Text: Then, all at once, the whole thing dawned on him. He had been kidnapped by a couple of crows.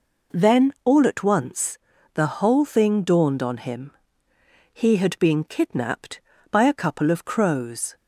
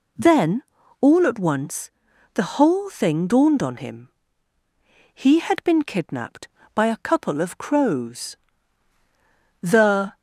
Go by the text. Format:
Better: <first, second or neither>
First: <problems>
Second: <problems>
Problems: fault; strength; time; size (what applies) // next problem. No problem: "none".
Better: first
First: none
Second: goes on to say "The"; from 9.6 s on; 0.56 s long